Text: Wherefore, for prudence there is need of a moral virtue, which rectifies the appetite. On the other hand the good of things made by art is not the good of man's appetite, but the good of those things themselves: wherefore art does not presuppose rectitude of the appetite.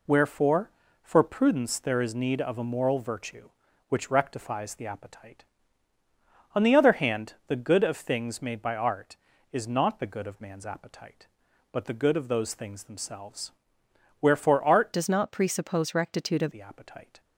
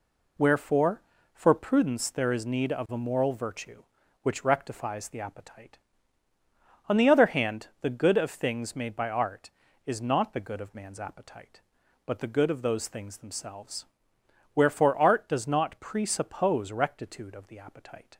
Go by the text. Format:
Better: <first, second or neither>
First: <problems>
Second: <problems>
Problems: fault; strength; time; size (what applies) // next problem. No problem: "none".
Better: second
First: changes voice from "does" to "of"; from 14.9 to 16.4 s; 1.5 s long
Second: none